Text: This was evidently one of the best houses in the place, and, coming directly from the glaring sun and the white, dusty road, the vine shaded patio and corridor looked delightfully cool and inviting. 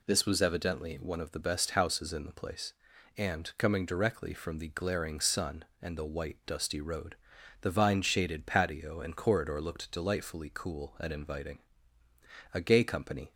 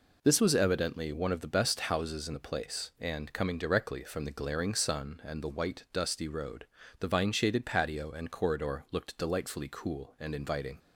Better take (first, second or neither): second